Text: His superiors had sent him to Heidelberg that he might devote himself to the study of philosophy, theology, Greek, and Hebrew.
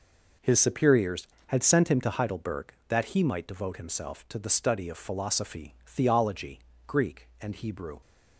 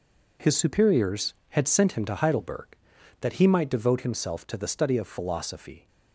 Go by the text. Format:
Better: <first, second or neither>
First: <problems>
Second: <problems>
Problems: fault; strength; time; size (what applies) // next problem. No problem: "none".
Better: first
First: none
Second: stops before "theology Greek and Hebrew"; at 5.8 s